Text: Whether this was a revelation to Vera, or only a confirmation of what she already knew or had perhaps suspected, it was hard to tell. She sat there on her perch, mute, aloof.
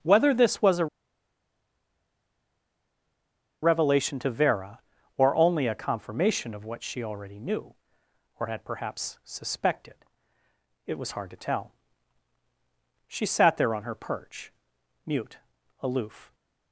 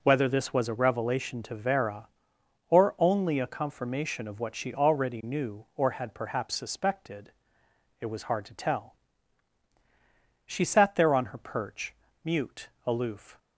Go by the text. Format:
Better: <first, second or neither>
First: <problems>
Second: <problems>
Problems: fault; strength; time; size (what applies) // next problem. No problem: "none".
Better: second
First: starts louder than the rest; strong; until 3.8 s; 7.5 dB // pauses between "a" and "revelation"; strong; at 0.8 s; 2.7 s long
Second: none